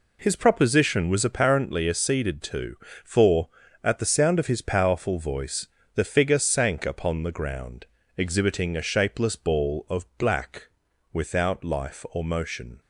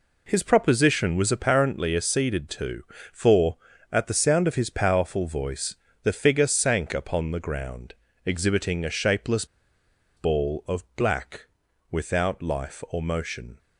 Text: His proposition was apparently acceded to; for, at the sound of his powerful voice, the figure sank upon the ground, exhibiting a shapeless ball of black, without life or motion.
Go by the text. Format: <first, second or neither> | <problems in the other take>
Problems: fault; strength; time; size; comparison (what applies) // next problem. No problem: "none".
first | pauses between "shapeless" and "ball"; noticeable; at 9.4 s; 0.71 s long